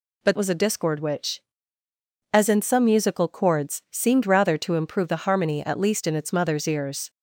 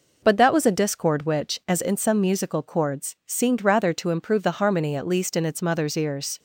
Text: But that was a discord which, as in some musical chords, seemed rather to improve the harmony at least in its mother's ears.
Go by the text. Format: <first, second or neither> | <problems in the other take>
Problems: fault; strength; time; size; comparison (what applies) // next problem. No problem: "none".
second | skips "that"; at 0.3 s